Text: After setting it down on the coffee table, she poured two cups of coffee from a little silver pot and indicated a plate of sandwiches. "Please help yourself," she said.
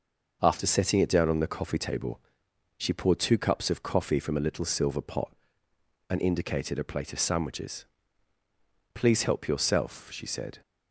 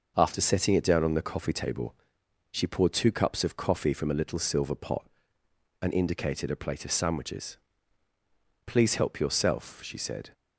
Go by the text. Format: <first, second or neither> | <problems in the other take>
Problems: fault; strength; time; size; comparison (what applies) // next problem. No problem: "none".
neither | starts louder than the rest; noticeable; the same in both